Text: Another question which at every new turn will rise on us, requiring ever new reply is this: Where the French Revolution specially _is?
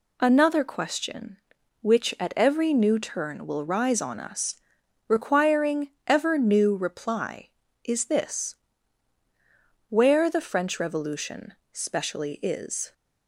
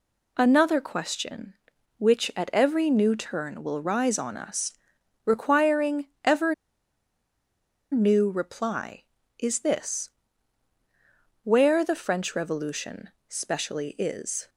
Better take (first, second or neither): first